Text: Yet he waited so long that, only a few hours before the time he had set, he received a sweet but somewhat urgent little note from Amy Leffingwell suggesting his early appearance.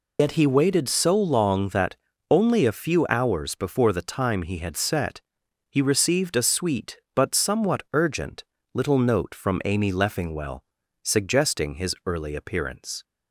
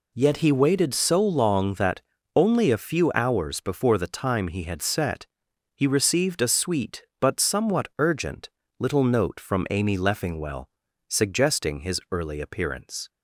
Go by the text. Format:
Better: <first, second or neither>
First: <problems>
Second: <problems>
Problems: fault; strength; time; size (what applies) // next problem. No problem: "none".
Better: second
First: loses the start of "Yet"; at 0.1 s; 105 ms // pauses between "urgent" and "little"; slight; at 8.4 s; 0.30 s long // pauses between "Leffingwell" and "suggesting"; at 10.6 s; 0.40 s long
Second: pauses between "urgent" and "little"; slight; at 8.4 s; 0.30 s long // pauses between "Leffingwell" and "suggesting"; at 10.6 s; 0.40 s long